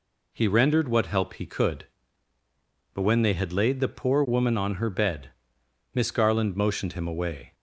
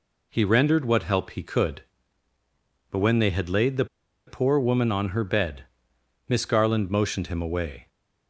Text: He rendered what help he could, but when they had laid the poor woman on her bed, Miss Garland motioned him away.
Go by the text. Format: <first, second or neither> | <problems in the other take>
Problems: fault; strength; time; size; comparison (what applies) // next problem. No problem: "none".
first | pauses between "the" and "poor"; at 3.8 s; 0.41 s long